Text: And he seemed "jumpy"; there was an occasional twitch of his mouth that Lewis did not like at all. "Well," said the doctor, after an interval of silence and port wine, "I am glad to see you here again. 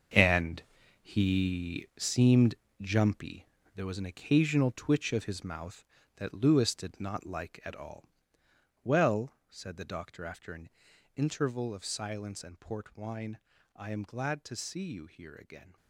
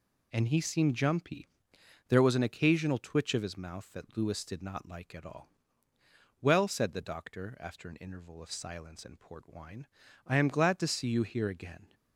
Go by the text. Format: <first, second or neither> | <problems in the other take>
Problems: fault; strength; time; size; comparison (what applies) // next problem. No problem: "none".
second | gets quieter; strong; throughout; 12.5 dB // pauses between "And" and "he"; at 0.6 s; 0.38 s long // pauses between "seemed" and "jumpy"; slight; at 2.5 s; 0.28 s long // pauses between "an" and "interval"; noticeable; at 10.6 s; 0.48 s long